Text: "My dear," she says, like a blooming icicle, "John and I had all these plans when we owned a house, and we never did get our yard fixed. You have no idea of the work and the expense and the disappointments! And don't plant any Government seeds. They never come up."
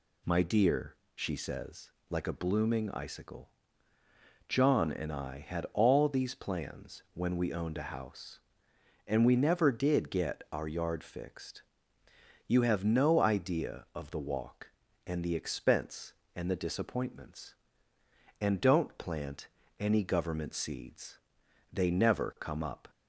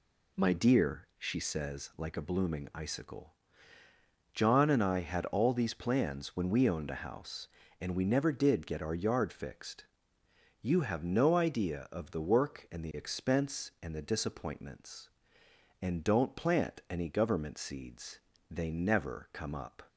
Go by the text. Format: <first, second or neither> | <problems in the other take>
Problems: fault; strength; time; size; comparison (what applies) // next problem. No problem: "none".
second | says "walk" for "work"; at 14.1 s // pauses between "plant" and "any"; slight; at 19.4 s; 0.30 s long